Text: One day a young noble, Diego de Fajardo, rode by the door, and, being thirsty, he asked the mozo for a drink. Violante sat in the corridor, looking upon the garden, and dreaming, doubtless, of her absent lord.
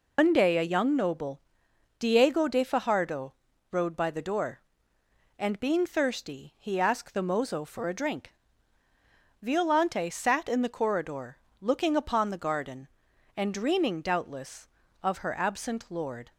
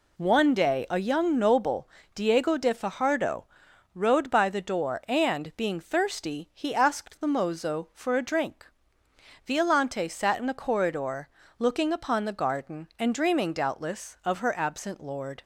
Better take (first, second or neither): second